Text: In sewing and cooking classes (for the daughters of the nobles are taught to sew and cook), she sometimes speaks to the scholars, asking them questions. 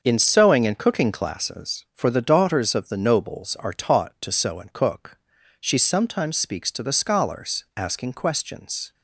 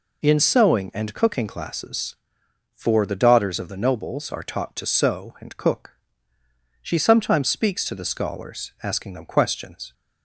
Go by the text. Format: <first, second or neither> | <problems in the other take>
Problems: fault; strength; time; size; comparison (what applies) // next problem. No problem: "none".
second | starts louder than the rest; until 1.0 s; 6.5 dB // skips "them"; at 8.1 s